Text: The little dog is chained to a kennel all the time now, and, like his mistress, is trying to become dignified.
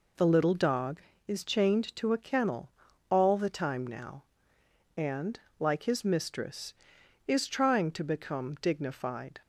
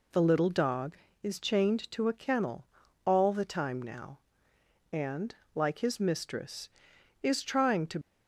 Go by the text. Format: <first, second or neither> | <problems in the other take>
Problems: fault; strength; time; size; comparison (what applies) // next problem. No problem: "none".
first | pauses between "kennel" and "all"; at 2.6 s; 0.42 s long; also in the first // stops before "become dignified"; at 8.0 s